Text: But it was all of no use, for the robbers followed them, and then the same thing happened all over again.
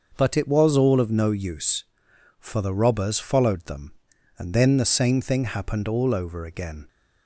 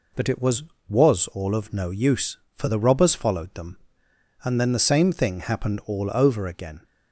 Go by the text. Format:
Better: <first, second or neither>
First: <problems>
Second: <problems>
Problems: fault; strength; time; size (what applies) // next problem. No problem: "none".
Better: first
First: none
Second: says "was" twice; at 0.8 s